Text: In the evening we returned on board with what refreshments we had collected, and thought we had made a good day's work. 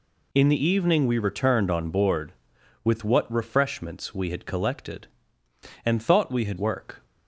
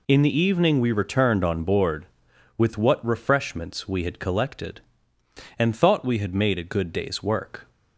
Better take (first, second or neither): second